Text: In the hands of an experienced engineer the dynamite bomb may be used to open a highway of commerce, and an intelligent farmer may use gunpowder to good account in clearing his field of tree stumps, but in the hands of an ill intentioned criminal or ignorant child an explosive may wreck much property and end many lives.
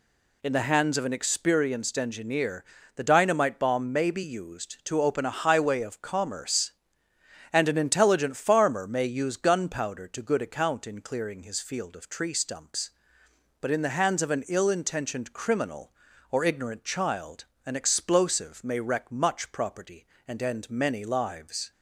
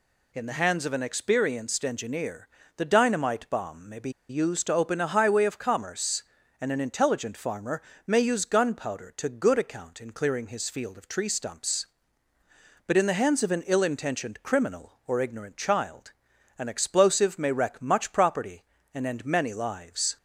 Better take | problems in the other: first | pauses between "engineer" and "the"; slight; at 2.4 s; 0.30 s long; slight in the first // pauses between "be" and "used"; slight; at 4.0 s; 0.19 s long // pauses between "farmer" and "may"; slight; at 7.8 s; 0.24 s long // pauses between "child" and "an"; at 16.1 s; 0.44 s long; slight in the first

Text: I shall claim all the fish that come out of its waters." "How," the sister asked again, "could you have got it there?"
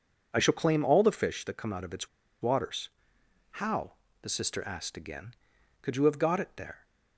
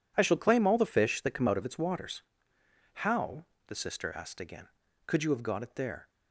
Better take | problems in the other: second | pauses between "its" and "waters"; slight; at 2.0 s; 0.33 s long

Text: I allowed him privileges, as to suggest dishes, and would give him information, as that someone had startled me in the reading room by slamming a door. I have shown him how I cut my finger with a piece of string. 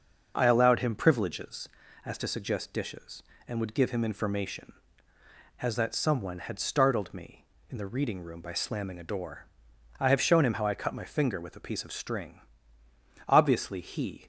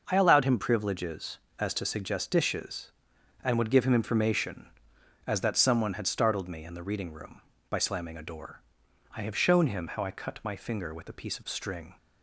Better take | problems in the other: second | starts louder than the rest; noticeable; until 1.3 s; 6 dB; noticeable in the second // goes on to say "Obviously he"; noticeable; from 13.2 s on; 0.98 s long

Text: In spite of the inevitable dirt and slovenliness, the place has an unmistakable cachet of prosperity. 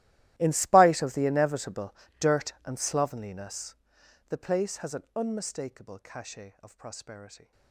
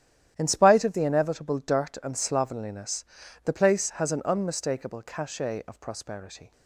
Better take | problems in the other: second | gets quieter; strong; throughout; 21 dB // starts louder than the rest; strong; until 1.3 s; 15 dB; strong in the second // pauses between "inevitable" and "dirt"; slight; at 1.9 s; 0.24 s long

